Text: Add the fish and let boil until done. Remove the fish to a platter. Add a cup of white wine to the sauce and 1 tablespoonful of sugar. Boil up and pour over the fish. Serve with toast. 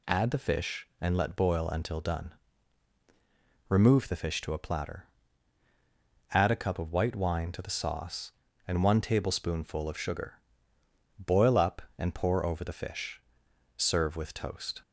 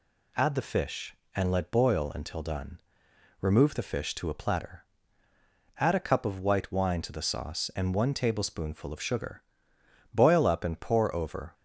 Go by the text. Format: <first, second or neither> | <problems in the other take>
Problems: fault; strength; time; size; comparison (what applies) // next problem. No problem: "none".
first | stops before "the fish Serve with toast"; at 11.5 s